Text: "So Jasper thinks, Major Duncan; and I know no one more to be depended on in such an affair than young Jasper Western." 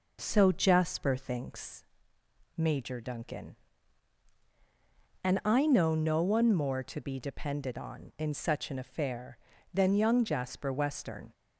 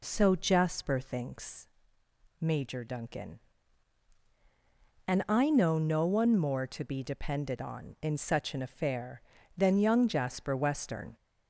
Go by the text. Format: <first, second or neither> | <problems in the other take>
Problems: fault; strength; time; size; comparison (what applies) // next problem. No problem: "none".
first | gets louder; slight; throughout; 2 dB